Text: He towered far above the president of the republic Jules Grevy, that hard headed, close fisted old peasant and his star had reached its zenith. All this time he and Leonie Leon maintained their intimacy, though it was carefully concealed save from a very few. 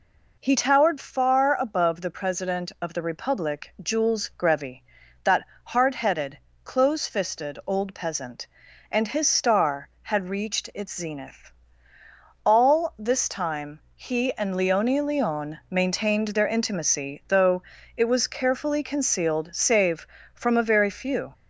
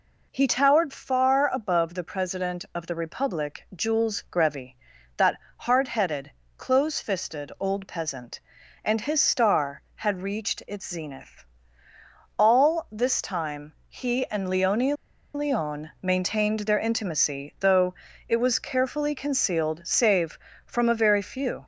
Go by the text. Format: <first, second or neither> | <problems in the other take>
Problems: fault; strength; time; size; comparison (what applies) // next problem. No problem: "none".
first | pauses between "that" and "hard"; slight; at 5.3 s; 0.18 s long; slight in the first // pauses between "Leonie" and "Leon"; at 14.9 s; 0.41 s long // pauses between "though" and "it"; slight; at 17.9 s; 0.34 s long; slight in the first